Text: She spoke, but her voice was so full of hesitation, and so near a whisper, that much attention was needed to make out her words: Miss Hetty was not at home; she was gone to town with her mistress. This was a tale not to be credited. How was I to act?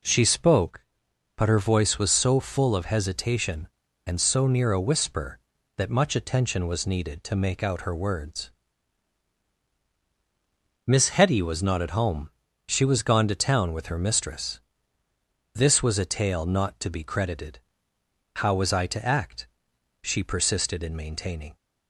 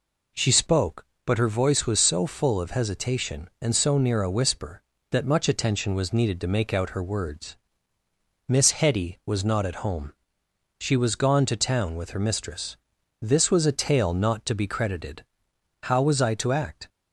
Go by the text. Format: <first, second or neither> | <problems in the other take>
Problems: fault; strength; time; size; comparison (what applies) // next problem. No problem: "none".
second | goes on to say "She persisted in maintaining"; from 20.0 s on; 1.5 s long